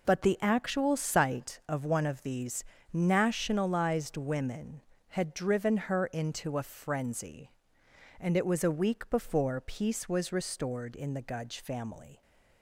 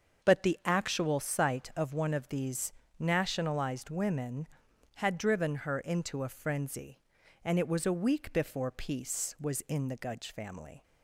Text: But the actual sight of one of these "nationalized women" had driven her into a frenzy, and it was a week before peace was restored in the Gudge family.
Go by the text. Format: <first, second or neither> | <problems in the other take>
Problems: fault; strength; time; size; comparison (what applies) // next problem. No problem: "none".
first | starts louder than the rest; until 1.3 s; 6.5 dB // pauses between "these" and "nationalized"; slight; at 2.7 s; 0.28 s long; slight in the first // skips "restored"; at 9.6 s